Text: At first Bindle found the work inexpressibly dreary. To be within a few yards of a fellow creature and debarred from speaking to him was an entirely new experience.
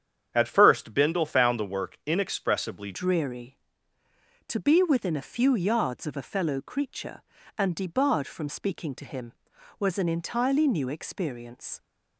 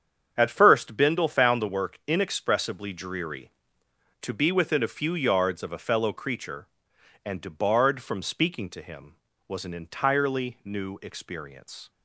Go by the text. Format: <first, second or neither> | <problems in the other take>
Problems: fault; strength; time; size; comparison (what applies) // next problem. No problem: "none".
second | starts louder than the rest; strong; until 1.3 s; 8.5 dB; strong in the second // changes voice at "dreary"; from 2.9 s on; 8.8 s long